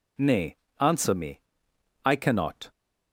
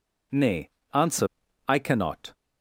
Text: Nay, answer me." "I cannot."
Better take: first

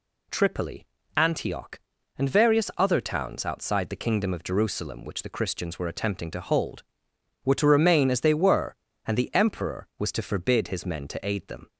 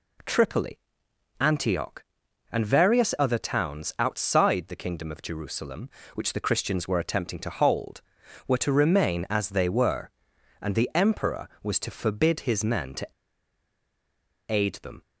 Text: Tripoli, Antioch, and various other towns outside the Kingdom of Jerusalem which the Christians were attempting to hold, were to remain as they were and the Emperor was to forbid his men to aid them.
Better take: first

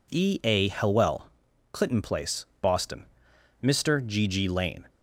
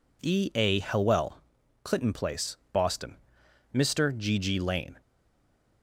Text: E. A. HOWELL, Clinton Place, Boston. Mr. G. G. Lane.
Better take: first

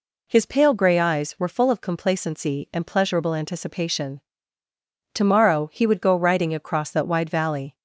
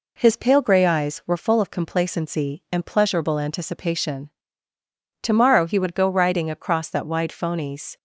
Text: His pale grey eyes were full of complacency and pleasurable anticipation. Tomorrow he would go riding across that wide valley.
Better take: first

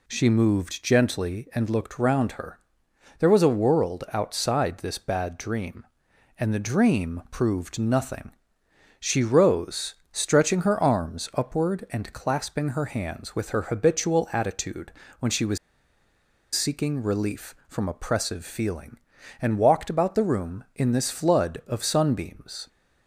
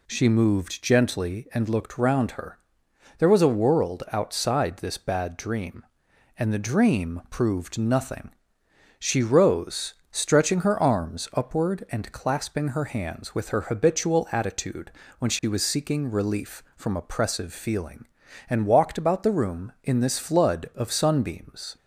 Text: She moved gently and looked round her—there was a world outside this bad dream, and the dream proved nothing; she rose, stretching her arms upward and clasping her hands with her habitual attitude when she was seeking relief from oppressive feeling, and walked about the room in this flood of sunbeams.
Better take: second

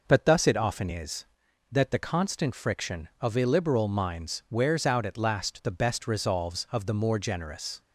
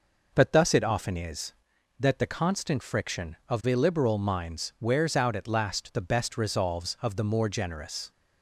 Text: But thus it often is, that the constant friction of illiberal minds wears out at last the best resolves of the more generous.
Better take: neither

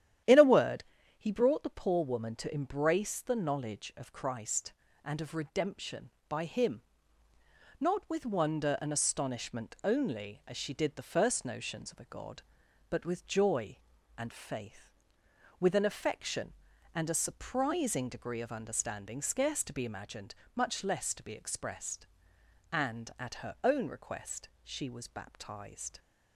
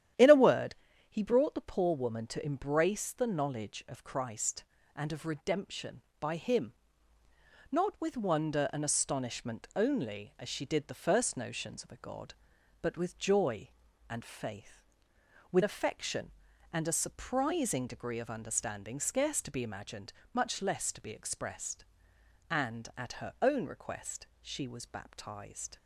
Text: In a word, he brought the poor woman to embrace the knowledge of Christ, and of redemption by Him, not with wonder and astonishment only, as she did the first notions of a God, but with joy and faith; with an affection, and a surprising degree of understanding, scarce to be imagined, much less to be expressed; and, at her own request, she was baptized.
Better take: first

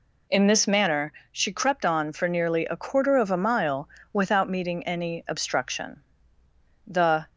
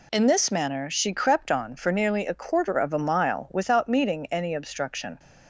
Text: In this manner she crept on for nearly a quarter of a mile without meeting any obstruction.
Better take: second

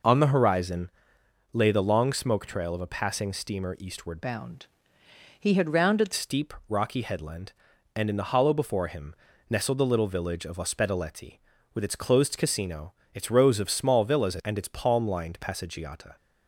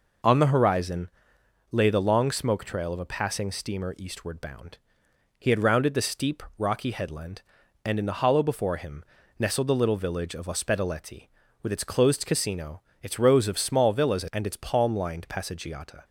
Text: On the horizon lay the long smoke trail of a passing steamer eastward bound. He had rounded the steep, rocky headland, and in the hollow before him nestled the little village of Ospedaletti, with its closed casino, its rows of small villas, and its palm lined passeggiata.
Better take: second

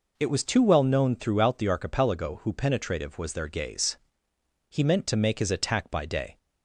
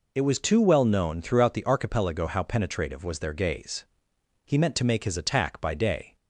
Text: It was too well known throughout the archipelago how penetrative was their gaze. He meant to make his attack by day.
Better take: second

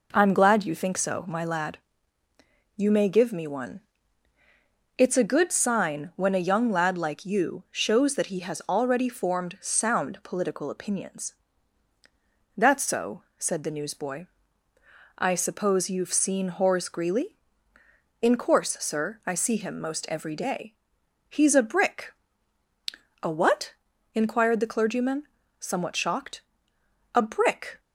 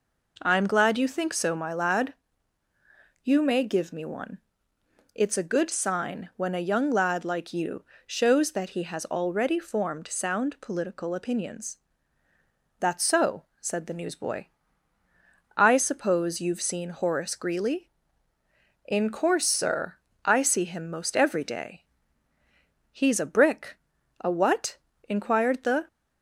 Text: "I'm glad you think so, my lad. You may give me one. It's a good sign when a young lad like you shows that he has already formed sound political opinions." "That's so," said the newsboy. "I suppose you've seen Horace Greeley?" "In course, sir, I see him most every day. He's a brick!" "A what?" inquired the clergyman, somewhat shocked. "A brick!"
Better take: first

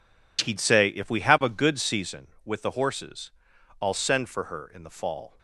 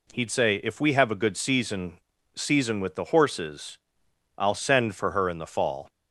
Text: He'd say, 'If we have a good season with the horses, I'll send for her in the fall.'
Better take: first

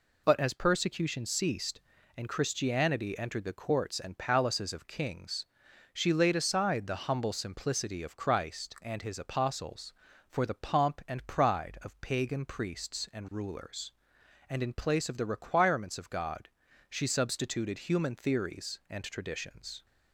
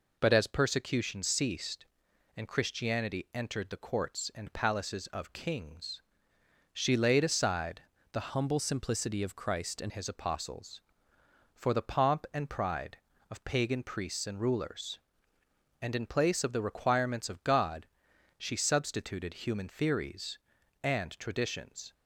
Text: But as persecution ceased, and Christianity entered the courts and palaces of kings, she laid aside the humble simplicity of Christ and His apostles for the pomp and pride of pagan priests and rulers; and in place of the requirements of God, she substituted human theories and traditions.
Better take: first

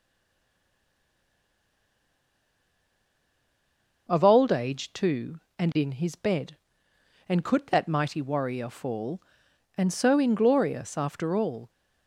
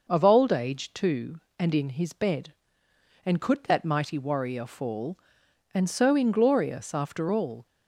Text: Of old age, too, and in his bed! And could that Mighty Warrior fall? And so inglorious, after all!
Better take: second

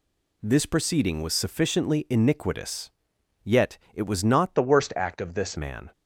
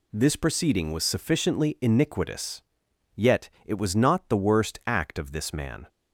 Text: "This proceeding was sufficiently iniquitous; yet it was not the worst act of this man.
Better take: second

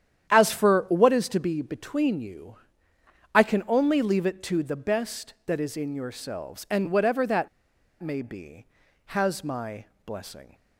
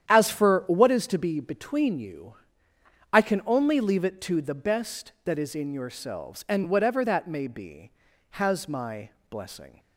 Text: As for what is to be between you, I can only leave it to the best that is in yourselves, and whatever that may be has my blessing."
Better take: second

